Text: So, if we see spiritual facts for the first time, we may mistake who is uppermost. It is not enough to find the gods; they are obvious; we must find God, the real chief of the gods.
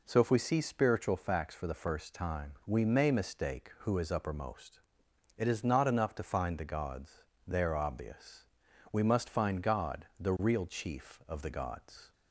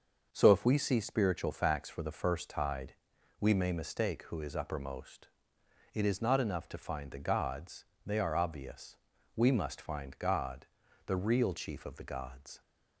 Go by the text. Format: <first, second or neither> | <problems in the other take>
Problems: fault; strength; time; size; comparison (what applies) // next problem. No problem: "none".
first | starts louder than the rest; until 1.3 s; 6 dB // says "tide" for "time"; at 2.4 s